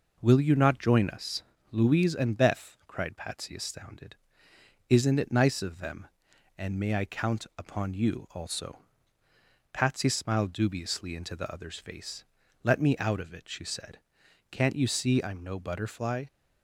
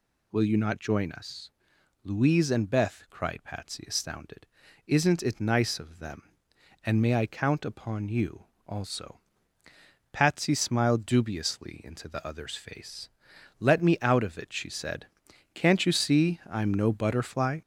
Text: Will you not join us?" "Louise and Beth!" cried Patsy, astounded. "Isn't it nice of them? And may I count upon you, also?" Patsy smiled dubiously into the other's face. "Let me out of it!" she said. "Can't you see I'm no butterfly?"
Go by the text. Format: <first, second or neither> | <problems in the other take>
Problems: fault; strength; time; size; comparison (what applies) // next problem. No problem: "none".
first | gets louder; throughout; 4 dB